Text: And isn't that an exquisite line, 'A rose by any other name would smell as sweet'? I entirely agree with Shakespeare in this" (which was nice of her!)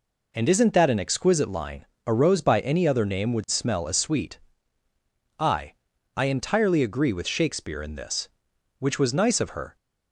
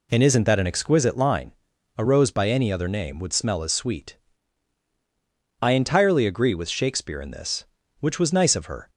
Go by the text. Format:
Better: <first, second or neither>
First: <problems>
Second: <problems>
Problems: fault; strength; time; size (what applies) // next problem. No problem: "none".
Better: second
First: says "I" twice; at 6.1 s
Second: none